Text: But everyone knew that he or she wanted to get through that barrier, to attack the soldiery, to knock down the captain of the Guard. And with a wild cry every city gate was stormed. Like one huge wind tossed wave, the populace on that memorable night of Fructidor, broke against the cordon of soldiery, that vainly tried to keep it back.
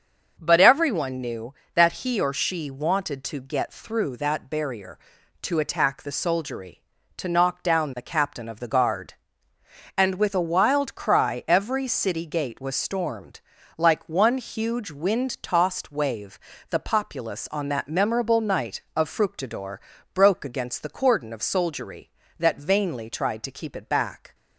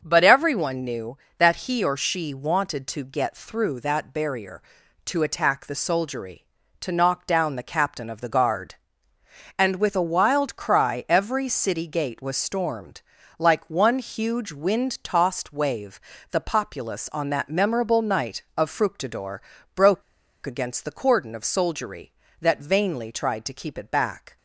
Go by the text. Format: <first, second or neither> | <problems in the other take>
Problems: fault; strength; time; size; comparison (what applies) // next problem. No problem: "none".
first | starts louder than the rest; until 1.0 s; 6.5 dB; also in the first // pauses between "broke" and "against"; at 20.0 s; 0.42 s long